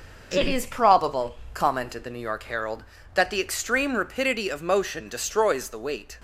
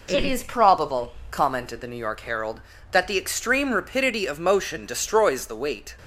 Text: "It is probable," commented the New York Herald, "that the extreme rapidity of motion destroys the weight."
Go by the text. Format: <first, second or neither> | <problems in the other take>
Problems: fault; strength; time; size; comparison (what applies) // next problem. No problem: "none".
second | gets quieter; noticeable; throughout; 5 dB